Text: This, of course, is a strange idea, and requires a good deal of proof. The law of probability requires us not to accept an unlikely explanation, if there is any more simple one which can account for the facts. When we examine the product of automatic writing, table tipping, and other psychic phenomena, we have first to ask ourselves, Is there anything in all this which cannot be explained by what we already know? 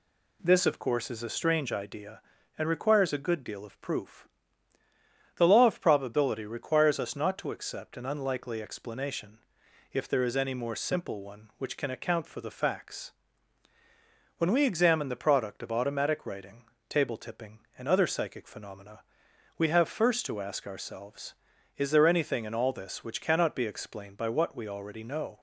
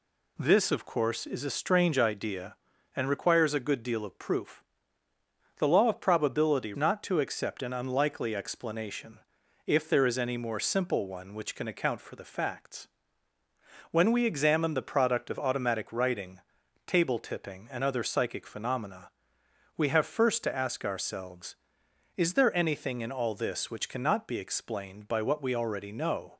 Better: first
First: none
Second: skips "requires us"; at 6.7 s

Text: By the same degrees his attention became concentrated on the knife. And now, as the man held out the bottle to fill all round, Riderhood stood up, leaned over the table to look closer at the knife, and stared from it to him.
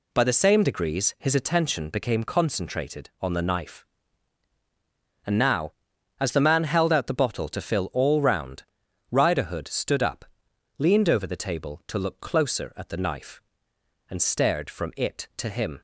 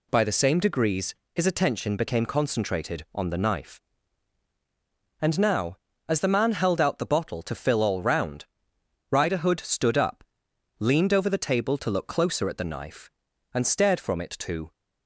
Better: first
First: none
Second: pauses between "degrees" and "his"; slight; at 1.1 s; 0.22 s long // stops before "him"; at 14.7 s

